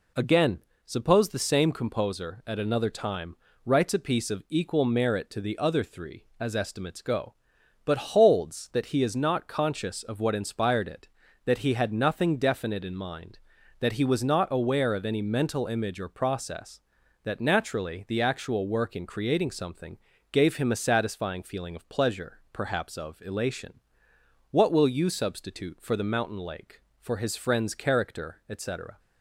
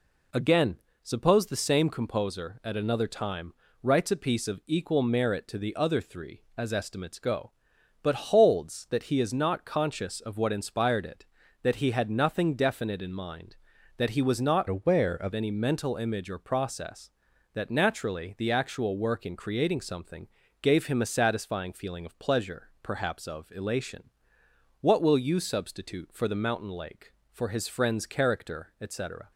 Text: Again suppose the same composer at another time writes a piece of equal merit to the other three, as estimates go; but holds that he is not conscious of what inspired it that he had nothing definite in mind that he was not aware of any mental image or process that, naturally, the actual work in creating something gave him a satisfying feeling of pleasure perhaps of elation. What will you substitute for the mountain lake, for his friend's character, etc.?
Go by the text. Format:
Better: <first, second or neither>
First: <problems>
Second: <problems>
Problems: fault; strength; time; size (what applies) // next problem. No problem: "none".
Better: first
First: pauses between "Again" and "suppose"; slight; at 0.5 s; 0.26 s long // pauses between "time" and "writes"; slight; at 3.3 s; 0.28 s long // pauses between "something" and "gave"; slight; at 19.9 s; 0.36 s long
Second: pauses between "Again" and "suppose"; slight; at 0.7 s; 0.26 s long // pauses between "time" and "writes"; slight; at 3.5 s; 0.28 s long // changes voice from "aware" to "of"; from 14.6 to 15.3 s; 0.7 s long // pauses between "something" and "gave"; slight; at 20.2 s; 0.36 s long